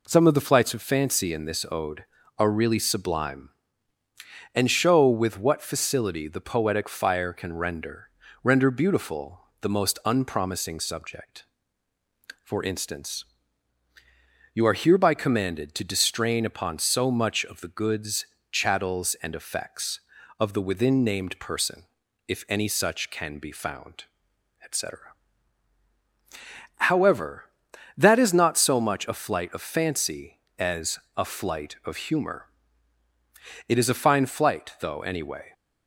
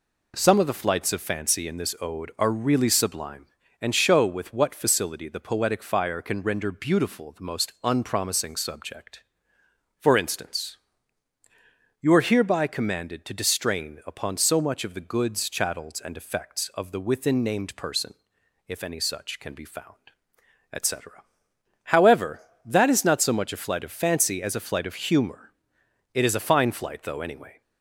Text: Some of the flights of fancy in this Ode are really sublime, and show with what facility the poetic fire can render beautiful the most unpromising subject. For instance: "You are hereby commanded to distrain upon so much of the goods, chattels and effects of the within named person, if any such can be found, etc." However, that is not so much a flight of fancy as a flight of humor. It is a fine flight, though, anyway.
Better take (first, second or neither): second